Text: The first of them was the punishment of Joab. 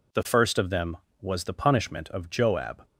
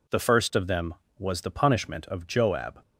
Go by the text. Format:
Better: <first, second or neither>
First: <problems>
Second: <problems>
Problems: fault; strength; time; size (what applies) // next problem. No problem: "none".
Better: neither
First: none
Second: none